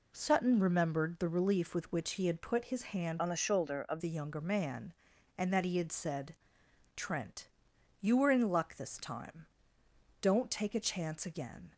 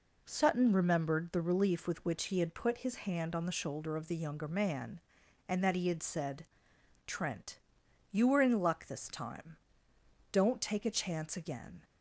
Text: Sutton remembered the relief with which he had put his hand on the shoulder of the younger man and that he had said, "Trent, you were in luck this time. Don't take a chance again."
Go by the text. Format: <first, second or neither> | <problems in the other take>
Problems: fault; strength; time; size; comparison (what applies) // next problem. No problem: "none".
second | changes voice from "on" to "of"; from 3.1 to 4.0 s; 0.9 s long